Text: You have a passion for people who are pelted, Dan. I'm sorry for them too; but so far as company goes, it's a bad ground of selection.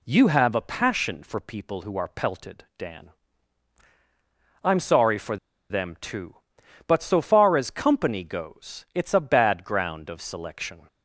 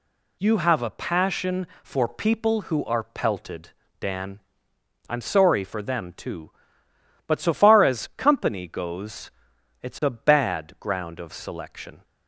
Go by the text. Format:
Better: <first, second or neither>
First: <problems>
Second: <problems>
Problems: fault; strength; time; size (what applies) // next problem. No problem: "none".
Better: second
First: pauses between "for" and "them"; slight; at 5.3 s; 0.34 s long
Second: none